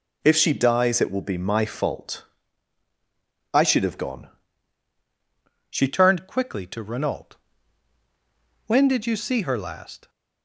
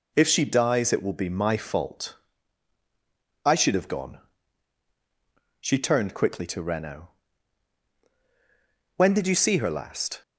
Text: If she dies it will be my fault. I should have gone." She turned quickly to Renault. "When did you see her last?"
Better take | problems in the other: second | changes voice at "turned"; from 5.8 s on; 4.2 s long

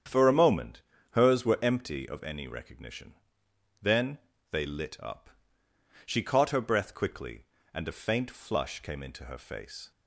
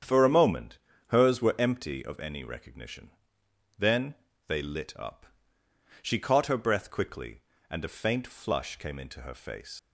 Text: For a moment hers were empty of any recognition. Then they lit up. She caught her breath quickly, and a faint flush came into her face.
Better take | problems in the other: first | starts louder than the rest; strong; until 1.3 s; 8 dB; strong in the first // pauses between "moment" and "hers"; slight; at 0.7 s; 0.28 s long; slight in the first // pauses between "Then" and "they"; slight; at 4.1 s; 0.32 s long; slight in the first // leaves "face" unfinished; at 9.7 s; 80 ms

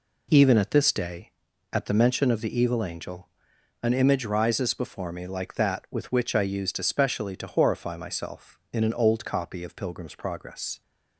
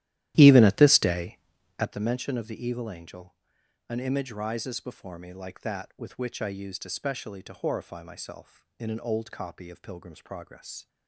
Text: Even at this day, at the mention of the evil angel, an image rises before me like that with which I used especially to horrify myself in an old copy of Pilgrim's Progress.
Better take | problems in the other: first | starts louder than the rest; strong; until 1.9 s; 13.5 dB

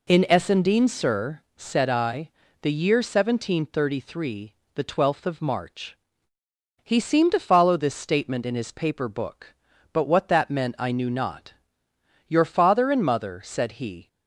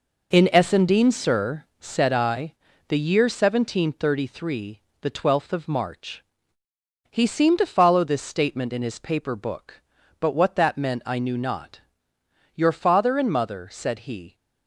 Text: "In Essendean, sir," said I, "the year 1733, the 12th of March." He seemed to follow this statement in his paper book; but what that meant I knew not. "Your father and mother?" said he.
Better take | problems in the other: first | gets quieter; strong; throughout; 7.5 dB

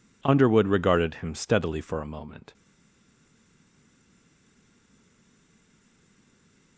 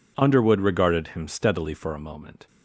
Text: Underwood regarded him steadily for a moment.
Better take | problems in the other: second | stays silent after the last word; strong; from 2.5 s on; 4.2 s long

